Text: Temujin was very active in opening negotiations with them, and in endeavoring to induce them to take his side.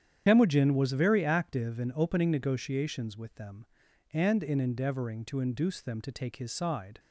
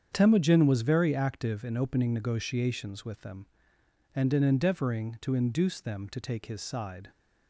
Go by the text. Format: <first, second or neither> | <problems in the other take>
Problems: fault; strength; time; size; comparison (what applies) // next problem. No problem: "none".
second | loses the start of "Temujin"; at 0.2 s; 55 ms // starts louder than the rest; strong; until 1.2 s; 9 dB; strong in the second